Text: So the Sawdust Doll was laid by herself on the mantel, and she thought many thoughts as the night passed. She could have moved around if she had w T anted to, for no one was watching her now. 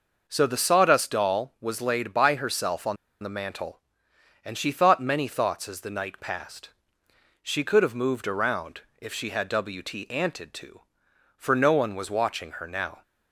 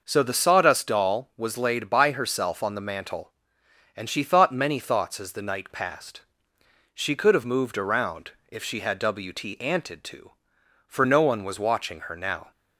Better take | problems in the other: second | pauses between "on" and "the"; slight; at 2.9 s; 0.27 s long // pauses between "around" and "if"; slight; at 8.8 s; 0.18 s long; slight in the second

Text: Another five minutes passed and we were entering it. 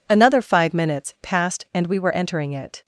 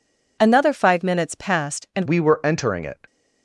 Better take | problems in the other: first | changes voice at "we"; from 2.0 s on; 1.0 s long

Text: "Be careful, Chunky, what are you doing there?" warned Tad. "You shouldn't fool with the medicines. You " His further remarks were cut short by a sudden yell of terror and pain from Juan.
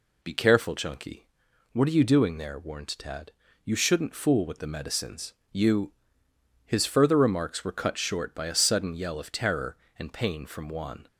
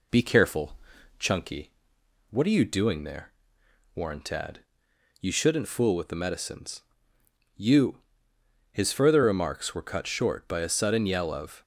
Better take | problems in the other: first | stops before "terror and pain from Juan"; at 11.6 s

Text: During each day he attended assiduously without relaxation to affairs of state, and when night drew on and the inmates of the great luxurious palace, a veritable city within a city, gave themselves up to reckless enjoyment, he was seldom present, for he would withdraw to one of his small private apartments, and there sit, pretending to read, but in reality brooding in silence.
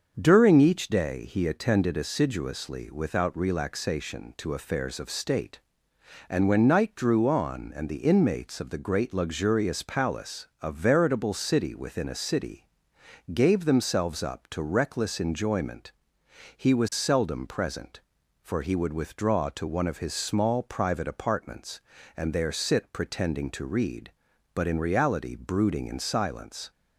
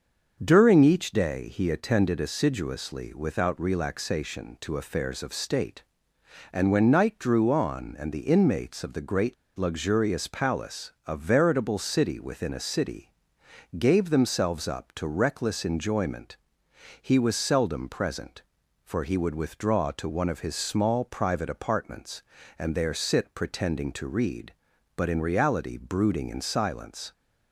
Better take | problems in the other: first | starts louder than the rest; until 1.4 s; 6.5 dB; also in the first // pauses between "great" and "luxurious"; slight; at 9.3 s; 0.21 s long

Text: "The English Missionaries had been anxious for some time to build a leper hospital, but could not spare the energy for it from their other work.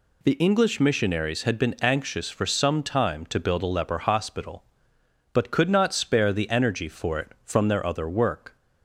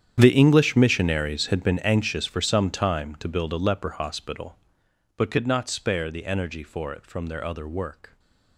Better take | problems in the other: first | gets quieter; strong; throughout; 18.5 dB // stays silent after the last word; slight; from 8.0 s on; 0.5 s long

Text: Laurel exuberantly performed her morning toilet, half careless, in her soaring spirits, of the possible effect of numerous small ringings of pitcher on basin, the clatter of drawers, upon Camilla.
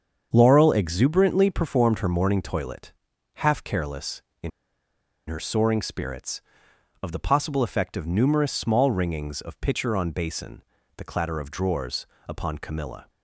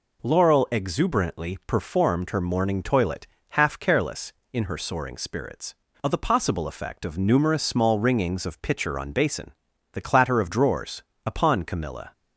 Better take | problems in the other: second | starts louder than the rest; until 1.3 s; 7 dB // pauses between "in" and "her"; noticeable; at 4.4 s; 0.79 s long

